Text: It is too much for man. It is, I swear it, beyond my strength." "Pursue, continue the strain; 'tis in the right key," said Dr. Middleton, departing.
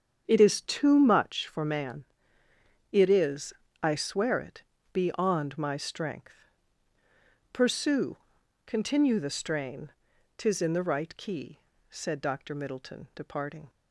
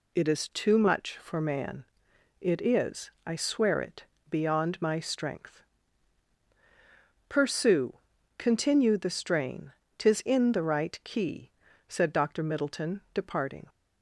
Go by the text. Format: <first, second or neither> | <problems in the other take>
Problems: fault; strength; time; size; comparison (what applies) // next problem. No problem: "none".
second | starts louder than the rest; strong; until 1.4 s; 7.5 dB